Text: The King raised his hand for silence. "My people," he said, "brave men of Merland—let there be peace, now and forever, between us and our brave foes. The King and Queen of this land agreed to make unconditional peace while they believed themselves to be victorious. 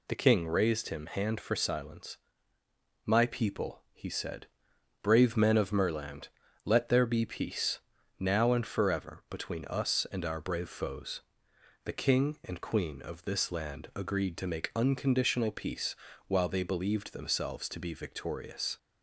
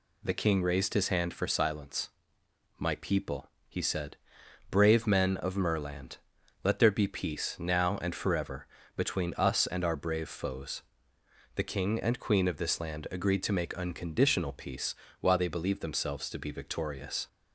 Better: second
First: says "him" for "his"; at 0.8 s // pauses between "peace" and "while"; slight; at 15.9 s; 0.32 s long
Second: pauses between "peace" and "while"; slight; at 14.9 s; 0.28 s long

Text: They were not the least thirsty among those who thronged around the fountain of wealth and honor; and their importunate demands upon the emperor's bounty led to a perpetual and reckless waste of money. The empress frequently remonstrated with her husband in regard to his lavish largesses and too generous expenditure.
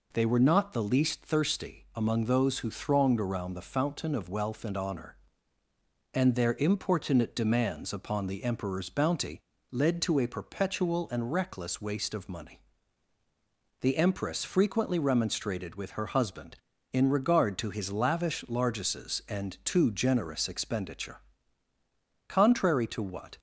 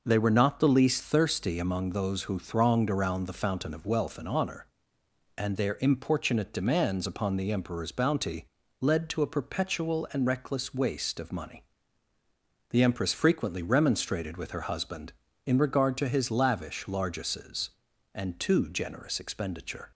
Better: second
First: pauses between "bounty" and "led"; slight; at 9.3 s; 0.32 s long // goes on to say "Contrary to what"; noticeable; from 22.2 s on; 1.1 s long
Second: pauses between "bounty" and "led"; slight; at 8.4 s; 0.34 s long

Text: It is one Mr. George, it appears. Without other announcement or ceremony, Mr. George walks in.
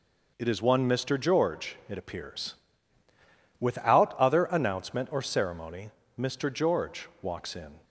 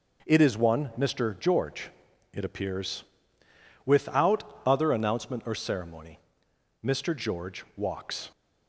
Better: first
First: none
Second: stops before "in"; at 8.3 s

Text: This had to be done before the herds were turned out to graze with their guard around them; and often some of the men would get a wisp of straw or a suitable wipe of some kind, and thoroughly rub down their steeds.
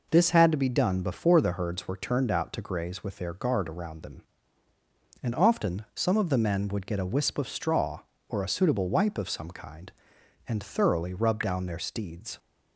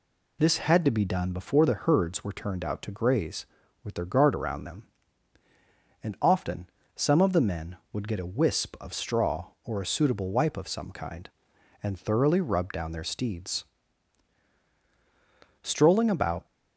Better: first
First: none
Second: pauses between "often" and "some"; slight; at 6.6 s; 0.26 s long // goes on to say "Strolling about"; noticeable; from 15.6 s on; 0.84 s long

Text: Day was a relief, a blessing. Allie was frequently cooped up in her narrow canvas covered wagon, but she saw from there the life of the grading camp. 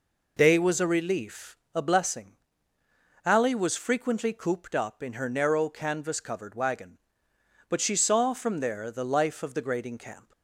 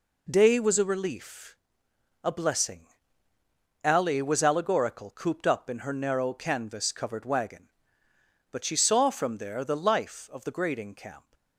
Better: first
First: none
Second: says "allegorical" for "frequently"; at 4.4 s

